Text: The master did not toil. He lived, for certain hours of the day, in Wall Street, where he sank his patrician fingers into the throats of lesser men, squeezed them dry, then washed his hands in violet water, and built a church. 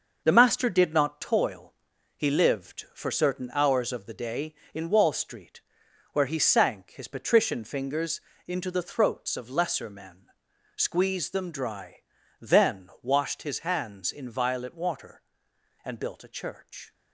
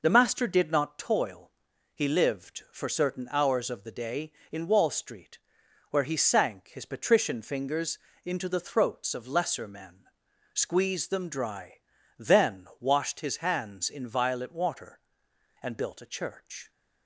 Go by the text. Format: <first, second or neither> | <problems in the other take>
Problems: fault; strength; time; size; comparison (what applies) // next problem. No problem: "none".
second | gets quieter; throughout; 7 dB // pauses between "fingers" and "into"; slight; at 8.1 s; 0.28 s long; slight in the second